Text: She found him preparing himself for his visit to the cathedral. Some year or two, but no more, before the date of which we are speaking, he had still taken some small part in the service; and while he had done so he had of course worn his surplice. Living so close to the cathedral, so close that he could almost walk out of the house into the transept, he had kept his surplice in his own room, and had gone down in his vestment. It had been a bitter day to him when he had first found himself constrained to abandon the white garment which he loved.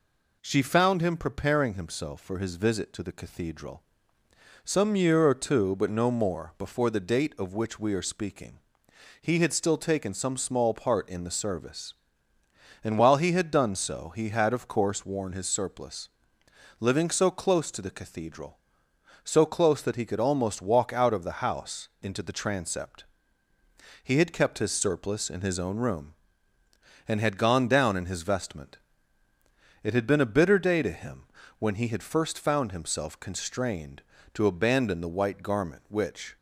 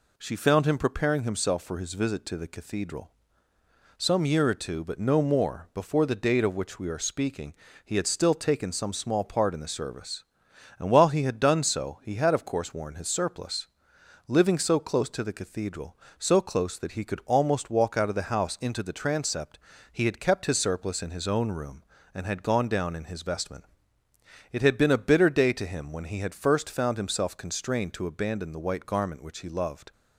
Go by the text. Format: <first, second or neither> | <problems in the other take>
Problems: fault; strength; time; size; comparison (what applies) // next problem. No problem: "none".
second | pauses between "him" and "when"; slight; at 31.2 s; 0.34 s long // stops before "he loved"; at 36.3 s